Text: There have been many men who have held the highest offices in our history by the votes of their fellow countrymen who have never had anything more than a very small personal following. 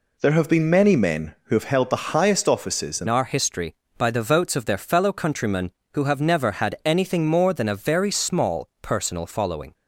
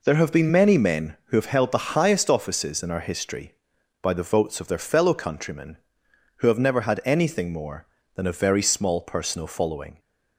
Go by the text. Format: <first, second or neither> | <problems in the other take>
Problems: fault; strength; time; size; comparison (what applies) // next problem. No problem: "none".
second | changes voice at "our"; from 3.0 s on; 6.7 s long // pauses between "small" and "personal"; slight; at 8.6 s; 0.16 s long